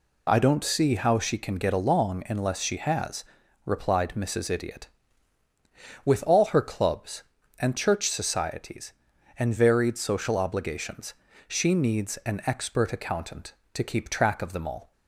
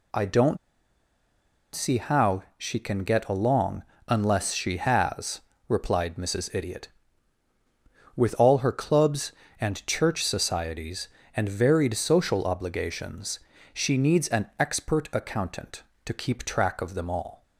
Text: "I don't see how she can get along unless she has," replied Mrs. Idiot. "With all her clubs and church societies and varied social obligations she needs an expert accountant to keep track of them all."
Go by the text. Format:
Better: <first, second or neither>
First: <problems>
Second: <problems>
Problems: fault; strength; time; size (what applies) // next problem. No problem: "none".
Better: first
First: pauses between "obligations" and "she"; slight; at 11.1 s; 0.32 s long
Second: pauses between "don't" and "see"; at 0.5 s; 1.1 s long // pauses between "along" and "unless"; slight; at 3.8 s; 0.24 s long // pauses between "obligations" and "she"; slight; at 13.4 s; 0.32 s long